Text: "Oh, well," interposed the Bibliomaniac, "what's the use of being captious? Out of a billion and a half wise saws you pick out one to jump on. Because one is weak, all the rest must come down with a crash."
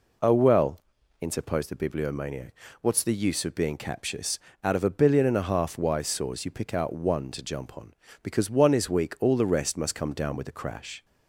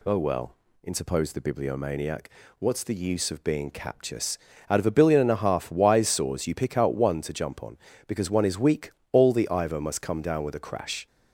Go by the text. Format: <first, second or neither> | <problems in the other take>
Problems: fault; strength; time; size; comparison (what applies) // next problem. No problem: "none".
first | says "ivor" for "rest"; at 9.5 s